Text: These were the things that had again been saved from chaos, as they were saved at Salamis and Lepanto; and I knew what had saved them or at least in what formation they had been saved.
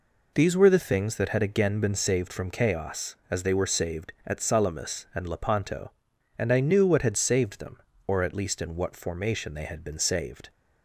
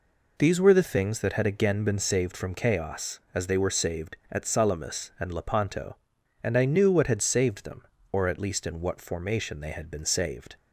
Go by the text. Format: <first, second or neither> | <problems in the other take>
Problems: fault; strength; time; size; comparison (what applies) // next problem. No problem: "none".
neither | none